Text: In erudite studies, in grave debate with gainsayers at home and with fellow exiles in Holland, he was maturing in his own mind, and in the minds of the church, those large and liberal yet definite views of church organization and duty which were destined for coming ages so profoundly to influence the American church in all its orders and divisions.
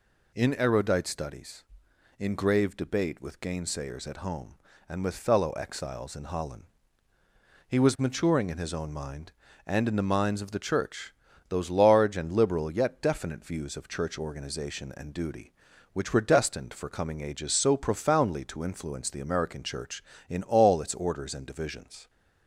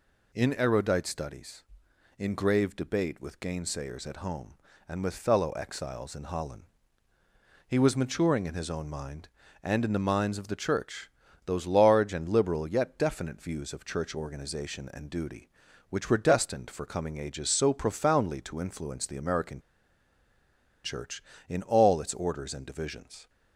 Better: first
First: none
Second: pauses between "American" and "church"; at 19.6 s; 1.2 s long

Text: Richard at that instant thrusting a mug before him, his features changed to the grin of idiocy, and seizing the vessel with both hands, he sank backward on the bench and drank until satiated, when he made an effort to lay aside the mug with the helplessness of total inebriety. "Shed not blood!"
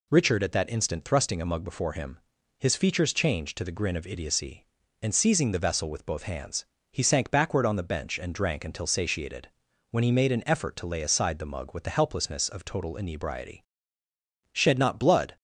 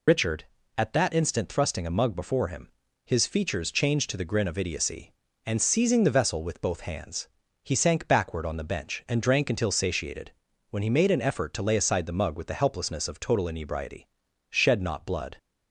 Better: first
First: none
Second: loses the start of "Richard"; at 0.0 s; 50 ms

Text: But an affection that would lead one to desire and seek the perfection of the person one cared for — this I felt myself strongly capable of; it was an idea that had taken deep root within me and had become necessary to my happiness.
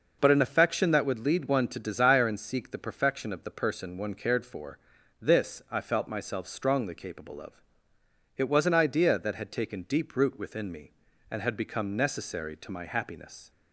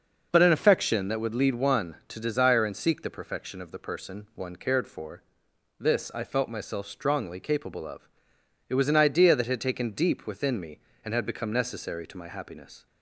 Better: first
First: none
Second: skips "root"; at 10.2 s

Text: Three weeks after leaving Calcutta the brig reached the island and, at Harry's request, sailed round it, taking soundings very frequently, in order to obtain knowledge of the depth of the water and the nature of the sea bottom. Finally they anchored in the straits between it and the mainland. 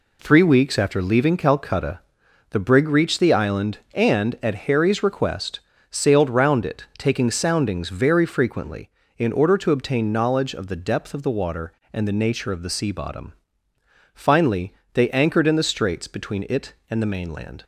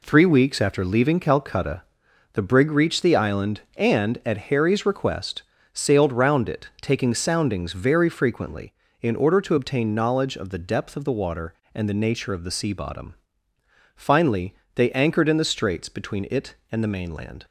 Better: neither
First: pauses between "Calcutta" and "the"; noticeable; at 2.0 s; 0.50 s long // pauses between "Finally" and "they"; slight; at 14.7 s; 0.20 s long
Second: pauses between "Calcutta" and "the"; noticeable; at 1.8 s; 0.50 s long // pauses between "Finally" and "they"; slight; at 14.5 s; 0.20 s long

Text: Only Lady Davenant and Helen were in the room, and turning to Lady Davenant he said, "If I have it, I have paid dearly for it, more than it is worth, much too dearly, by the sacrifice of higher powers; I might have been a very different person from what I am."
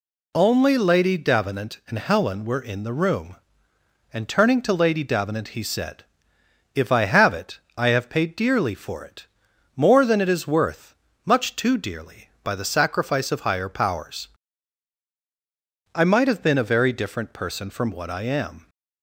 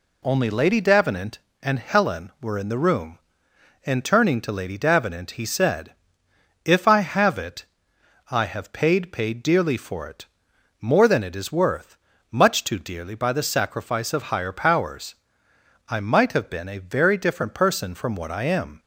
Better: first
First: none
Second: says "paid" twice; at 9.1 s

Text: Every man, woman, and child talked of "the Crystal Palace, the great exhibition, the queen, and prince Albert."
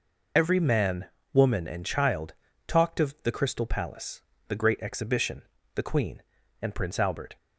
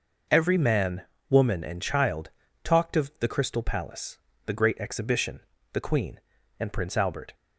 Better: second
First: loses the start of "Every"; at 0.3 s; 40 ms // pauses between "child" and "talked"; slight; at 2.3 s; 0.34 s long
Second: pauses between "child" and "talked"; slight; at 2.3 s; 0.34 s long

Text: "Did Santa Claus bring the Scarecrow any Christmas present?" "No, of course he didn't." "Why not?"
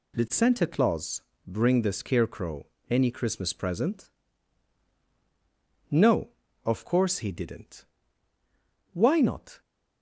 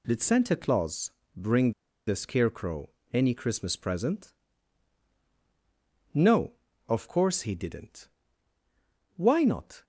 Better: first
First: pauses between "Claus" and "bring"; slight; at 1.2 s; 0.26 s long // pauses between "Scarecrow" and "any"; slight; at 2.6 s; 0.24 s long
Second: pauses between "Claus" and "bring"; slight; at 1.0 s; 0.26 s long // pauses between "bring" and "the"; slight; at 1.7 s; 0.35 s long // pauses between "Scarecrow" and "any"; slight; at 2.8 s; 0.24 s long

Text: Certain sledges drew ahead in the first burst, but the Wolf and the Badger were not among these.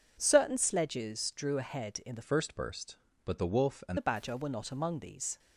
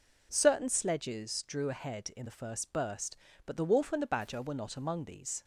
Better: second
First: changes voice from "first" to "and"; from 2.2 to 3.9 s; 1.7 s long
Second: none

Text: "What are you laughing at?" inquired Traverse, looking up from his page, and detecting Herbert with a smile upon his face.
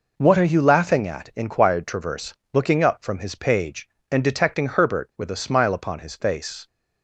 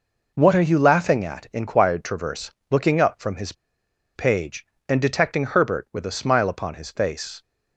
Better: first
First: none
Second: pauses between "his" and "page"; noticeable; at 3.5 s; 0.62 s long

